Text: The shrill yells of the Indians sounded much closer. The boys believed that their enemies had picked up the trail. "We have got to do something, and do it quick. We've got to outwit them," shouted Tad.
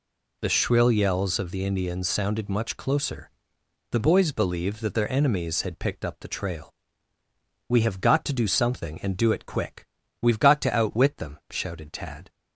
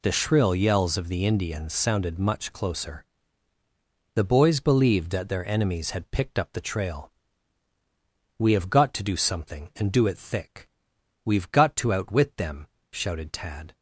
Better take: first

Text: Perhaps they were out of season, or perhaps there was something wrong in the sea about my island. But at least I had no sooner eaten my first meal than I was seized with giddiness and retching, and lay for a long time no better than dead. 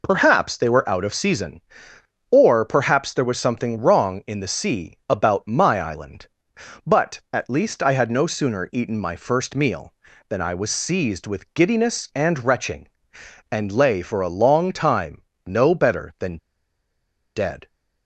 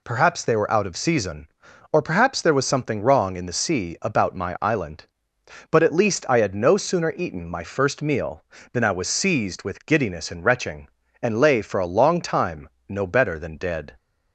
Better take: second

